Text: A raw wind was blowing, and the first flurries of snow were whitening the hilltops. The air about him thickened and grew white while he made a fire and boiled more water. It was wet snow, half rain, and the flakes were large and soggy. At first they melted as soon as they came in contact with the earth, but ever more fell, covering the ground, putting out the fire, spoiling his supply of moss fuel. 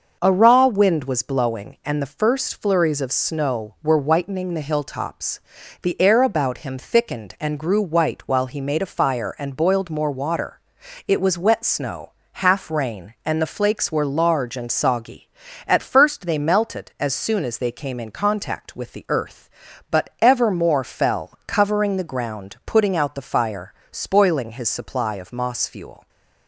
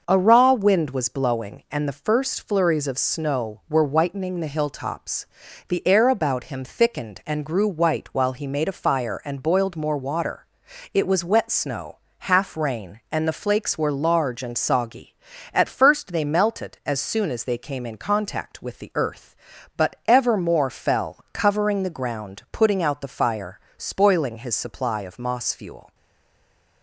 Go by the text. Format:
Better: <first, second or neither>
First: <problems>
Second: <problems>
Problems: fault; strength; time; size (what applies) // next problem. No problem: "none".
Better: first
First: starts louder than the rest; until 1.2 s; 6.5 dB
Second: starts louder than the rest; until 1.0 s; 6.5 dB // stays silent after the last word; slight; from 25.9 s on; 0.9 s long